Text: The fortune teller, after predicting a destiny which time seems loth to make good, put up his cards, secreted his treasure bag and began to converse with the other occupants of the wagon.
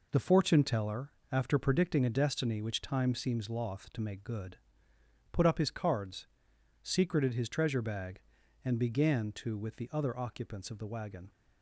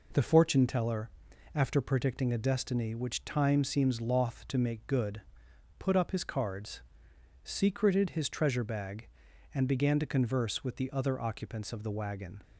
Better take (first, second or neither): second